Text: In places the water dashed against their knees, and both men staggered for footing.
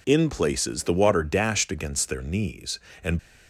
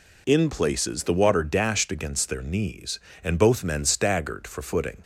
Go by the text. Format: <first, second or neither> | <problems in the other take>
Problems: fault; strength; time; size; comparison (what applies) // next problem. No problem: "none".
second | stops before "both men staggered for footing"; at 3.1 s